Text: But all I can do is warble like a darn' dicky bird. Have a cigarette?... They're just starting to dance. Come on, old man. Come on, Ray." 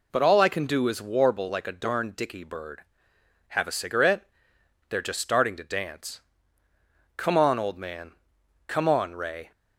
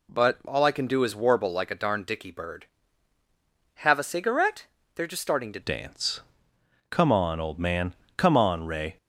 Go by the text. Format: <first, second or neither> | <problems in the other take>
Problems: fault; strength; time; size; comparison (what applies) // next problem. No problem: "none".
first | changes voice at "dance"; from 5.6 s on; 3.3 s long